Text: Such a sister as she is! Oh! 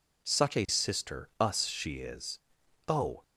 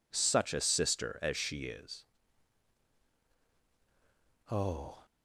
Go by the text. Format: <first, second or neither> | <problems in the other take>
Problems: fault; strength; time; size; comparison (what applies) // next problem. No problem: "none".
second | says "us" for "as"; at 1.3 s